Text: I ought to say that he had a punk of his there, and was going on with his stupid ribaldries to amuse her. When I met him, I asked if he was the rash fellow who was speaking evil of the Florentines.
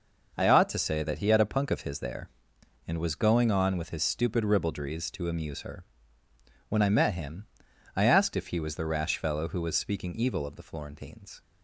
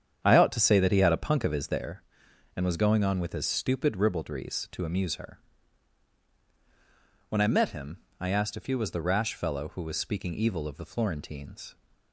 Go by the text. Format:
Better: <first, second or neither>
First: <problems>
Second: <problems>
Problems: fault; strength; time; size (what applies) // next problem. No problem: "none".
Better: first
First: none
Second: starts louder than the rest; strong; until 1.9 s; 8.5 dB